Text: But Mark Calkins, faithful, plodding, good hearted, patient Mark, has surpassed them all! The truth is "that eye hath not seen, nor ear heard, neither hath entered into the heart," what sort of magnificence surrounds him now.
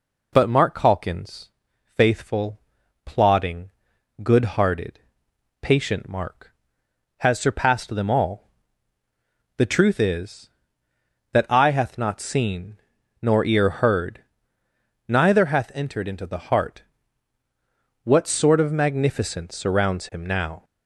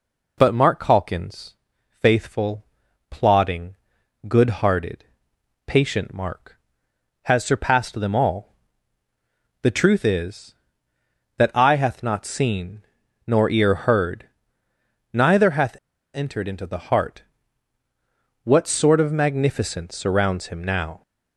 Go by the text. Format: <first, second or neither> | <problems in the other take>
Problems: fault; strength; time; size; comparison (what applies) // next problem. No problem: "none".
first | pauses between "hath" and "entered"; at 15.7 s; 0.41 s long